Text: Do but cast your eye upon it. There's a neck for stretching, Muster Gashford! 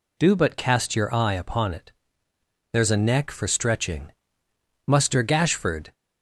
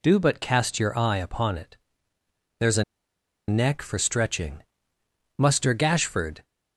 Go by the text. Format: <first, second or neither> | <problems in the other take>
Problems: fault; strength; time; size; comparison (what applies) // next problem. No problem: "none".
first | pauses between "a" and "neck"; noticeable; at 2.8 s; 0.65 s long